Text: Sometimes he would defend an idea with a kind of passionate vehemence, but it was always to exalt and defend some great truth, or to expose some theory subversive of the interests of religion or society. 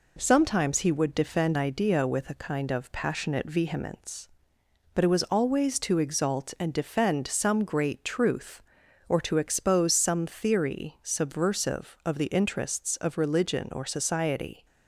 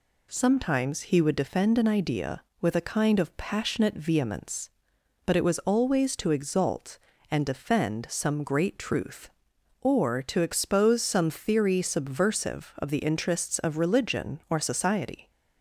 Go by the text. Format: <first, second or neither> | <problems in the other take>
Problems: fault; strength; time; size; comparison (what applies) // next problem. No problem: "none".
second | skips "an"; at 1.5 s